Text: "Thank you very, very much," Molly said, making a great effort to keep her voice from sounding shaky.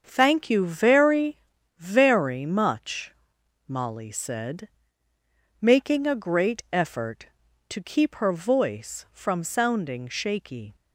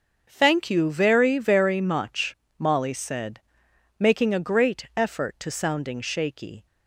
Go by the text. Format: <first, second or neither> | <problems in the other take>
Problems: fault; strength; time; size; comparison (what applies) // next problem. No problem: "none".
first | starts louder than the rest; until 1.3 s; 7 dB; also in the first // skips "keep her voice from"; at 5.5 s